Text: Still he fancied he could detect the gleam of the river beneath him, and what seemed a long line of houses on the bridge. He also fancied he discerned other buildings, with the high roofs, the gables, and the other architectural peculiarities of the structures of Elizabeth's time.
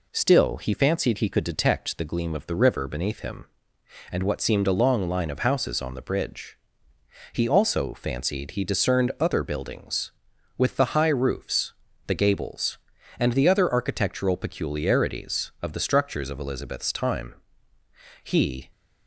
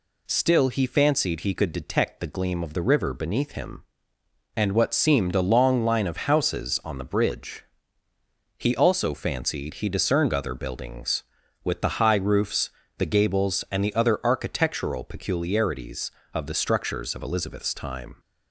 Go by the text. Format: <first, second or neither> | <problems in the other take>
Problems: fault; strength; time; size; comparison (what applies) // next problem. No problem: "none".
second | goes on to say "He"; slight; from 18.2 s on; 0.46 s long